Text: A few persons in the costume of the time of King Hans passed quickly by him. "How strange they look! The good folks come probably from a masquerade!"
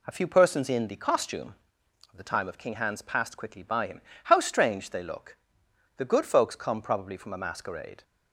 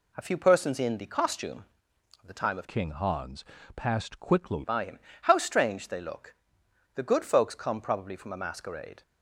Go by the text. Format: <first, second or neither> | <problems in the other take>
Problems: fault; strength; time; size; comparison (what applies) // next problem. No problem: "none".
first | changes voice from "King" to "quickly"; from 2.6 to 4.6 s; 2.0 s long // pauses between "Hans" and "passed"; slight; at 3.4 s; 0.32 s long